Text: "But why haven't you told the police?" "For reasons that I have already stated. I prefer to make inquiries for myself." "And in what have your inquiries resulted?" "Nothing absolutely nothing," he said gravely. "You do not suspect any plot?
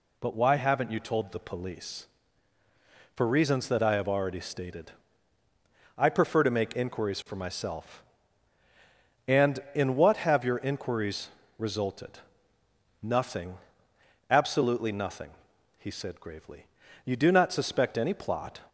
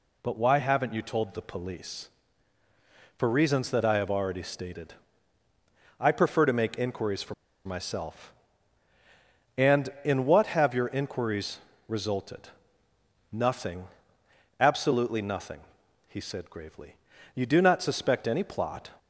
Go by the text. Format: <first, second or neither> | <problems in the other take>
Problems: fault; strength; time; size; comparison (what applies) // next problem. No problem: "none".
first | pauses between "for" and "myself"; slight; at 7.3 s; 0.31 s long // pauses between "inquiries" and "resulted"; slight; at 11.5 s; 0.28 s long; slight in the first // pauses between "Nothing" and "absolutely"; noticeable; at 13.8 s; 0.72 s long; noticeable in the first